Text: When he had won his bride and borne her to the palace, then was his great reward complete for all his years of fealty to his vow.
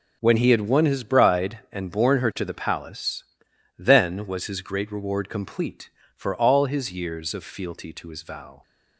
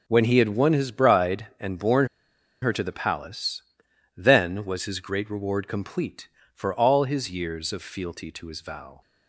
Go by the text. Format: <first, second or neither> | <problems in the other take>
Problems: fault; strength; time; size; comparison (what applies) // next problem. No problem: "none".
first | pauses between "borne" and "her"; noticeable; at 2.0 s; 0.55 s long